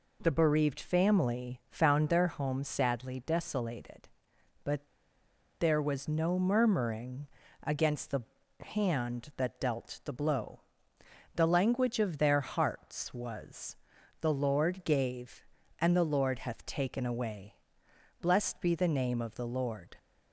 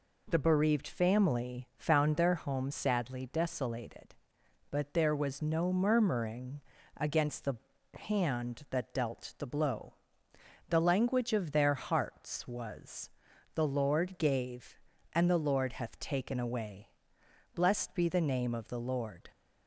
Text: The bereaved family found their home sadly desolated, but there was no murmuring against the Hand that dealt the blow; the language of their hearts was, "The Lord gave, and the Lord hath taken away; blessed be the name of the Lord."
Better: second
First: pauses between "but" and "there"; noticeable; at 4.8 s; 0.73 s long // pauses between "murmuring" and "against"; at 7.2 s; 0.38 s long // pauses between "the" and "Hand"; at 8.2 s; 0.38 s long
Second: pauses between "murmuring" and "against"; at 6.5 s; 0.38 s long // pauses between "the" and "Hand"; at 7.5 s; 0.38 s long

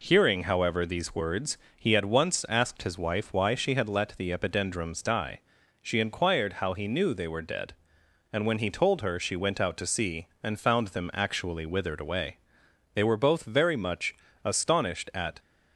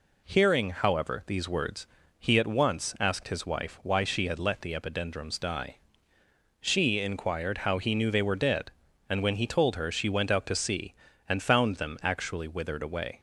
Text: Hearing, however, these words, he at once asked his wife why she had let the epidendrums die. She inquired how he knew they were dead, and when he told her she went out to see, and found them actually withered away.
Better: second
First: goes on to say "They were both very much astonished at"; strong; from 12.9 s on; 2.4 s long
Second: none

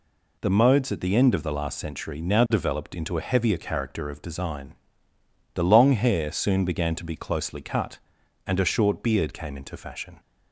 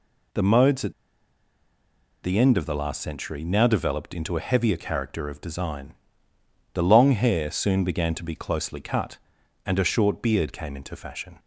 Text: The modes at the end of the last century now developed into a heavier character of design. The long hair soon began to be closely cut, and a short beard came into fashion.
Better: first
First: none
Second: pauses between "at" and "the"; strong; at 0.9 s; 1.3 s long

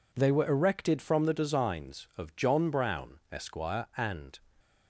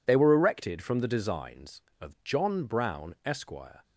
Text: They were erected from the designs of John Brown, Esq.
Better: second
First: goes on to say "and"; slight; from 3.9 s on; 0.42 s long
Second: none

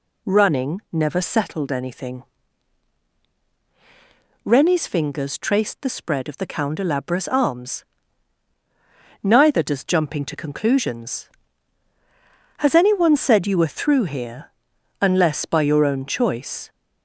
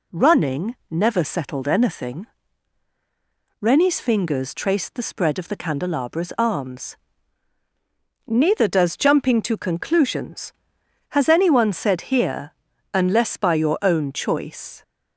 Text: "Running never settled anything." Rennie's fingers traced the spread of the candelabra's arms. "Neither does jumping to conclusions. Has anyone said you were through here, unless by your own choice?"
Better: first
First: none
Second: pauses between "Running" and "never"; slight; at 0.7 s; 0.16 s long // skips "you were through"; at 12.1 s

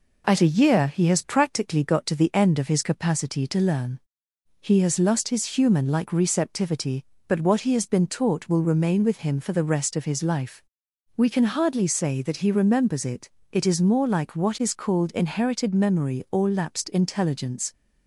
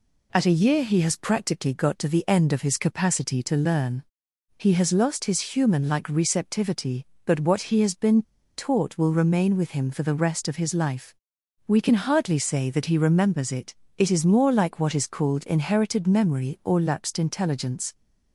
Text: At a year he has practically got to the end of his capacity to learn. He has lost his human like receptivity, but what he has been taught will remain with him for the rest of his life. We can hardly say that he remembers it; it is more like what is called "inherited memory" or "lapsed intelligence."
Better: first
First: none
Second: pauses between "been" and "taught"; slight; at 8.2 s; 0.35 s long

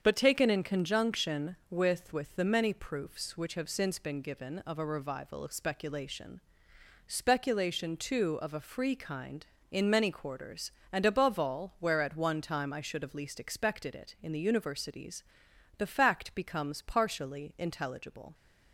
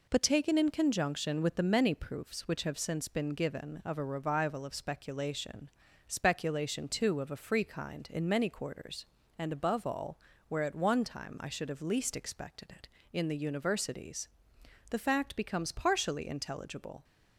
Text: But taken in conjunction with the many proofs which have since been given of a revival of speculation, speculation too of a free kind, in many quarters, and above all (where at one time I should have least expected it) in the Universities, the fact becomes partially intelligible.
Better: second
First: starts louder than the rest; strong; until 1.0 s; 7 dB // says "with" twice; at 2.1 s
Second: none

